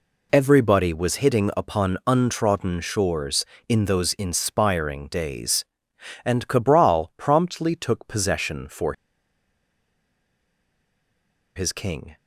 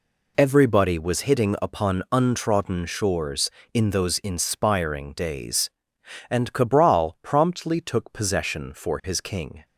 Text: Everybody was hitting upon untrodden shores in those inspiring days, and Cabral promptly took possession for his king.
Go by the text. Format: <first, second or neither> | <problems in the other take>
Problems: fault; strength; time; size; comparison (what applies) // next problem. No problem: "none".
second | pauses between "for" and "his"; strong; at 8.9 s; 2.6 s long